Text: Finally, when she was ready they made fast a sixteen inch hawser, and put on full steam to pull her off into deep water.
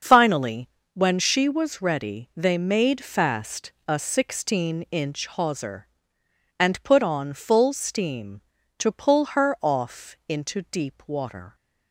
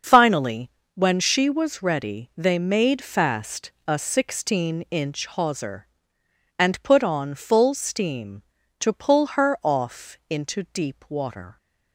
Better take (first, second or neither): neither